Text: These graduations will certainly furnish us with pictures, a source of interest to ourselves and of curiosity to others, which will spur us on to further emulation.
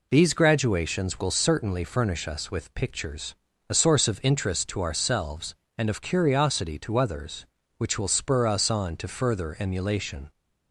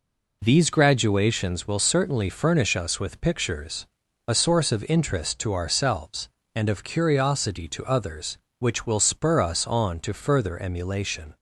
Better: neither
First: none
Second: none

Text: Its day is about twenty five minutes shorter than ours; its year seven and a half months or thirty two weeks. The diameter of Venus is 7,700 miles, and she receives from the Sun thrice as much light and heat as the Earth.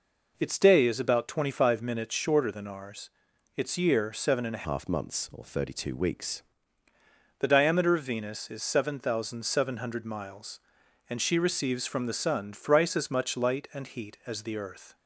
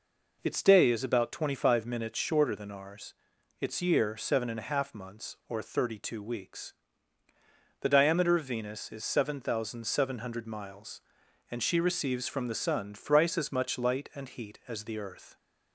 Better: second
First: changes voice from "half" to "weeks"; from 4.6 to 6.4 s; 1.8 s long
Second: none

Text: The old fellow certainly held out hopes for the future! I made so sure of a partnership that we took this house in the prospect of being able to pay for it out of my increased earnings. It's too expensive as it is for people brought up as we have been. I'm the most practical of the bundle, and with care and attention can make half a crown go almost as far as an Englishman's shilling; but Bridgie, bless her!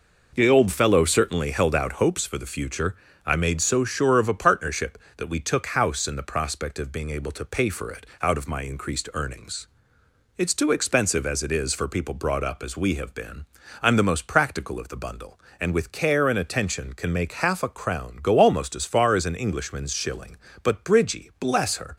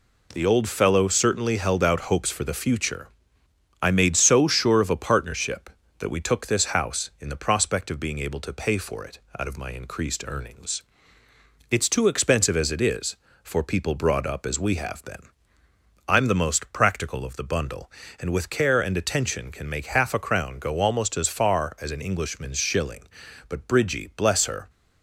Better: second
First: skips "this"; at 5.6 s // pauses between "it" and "out"; slight; at 8.0 s; 0.16 s long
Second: pauses between "it" and "out"; slight; at 9.1 s; 0.18 s long

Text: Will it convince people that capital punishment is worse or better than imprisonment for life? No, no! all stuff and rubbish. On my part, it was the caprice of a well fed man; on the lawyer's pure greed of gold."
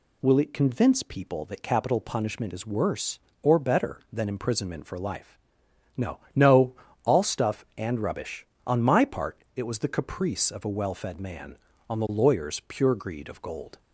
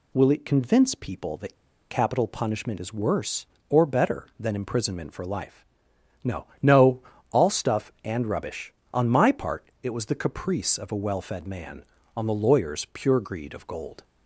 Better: first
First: none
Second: pauses between "that" and "capital"; slight; at 1.5 s; 0.35 s long

